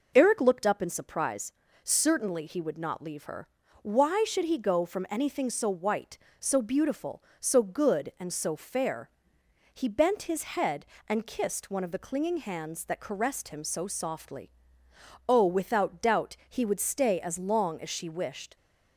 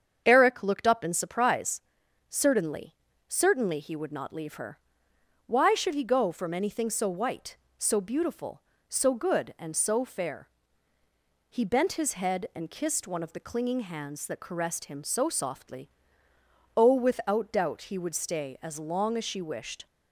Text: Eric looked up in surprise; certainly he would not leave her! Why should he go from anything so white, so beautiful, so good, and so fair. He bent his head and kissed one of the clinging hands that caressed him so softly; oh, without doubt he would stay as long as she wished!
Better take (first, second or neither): first